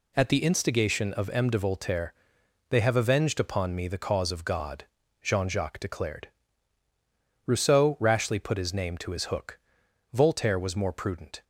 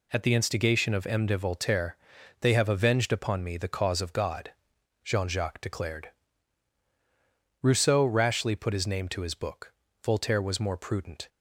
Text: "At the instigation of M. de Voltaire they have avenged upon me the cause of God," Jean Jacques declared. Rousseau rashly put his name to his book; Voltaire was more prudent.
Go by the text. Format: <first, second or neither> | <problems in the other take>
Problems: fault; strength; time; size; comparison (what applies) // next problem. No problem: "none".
second | pauses between "Voltaire" and "they"; noticeable; at 2.1 s; 0.54 s long; also in the second // says "hook" for "book"; at 9.2 s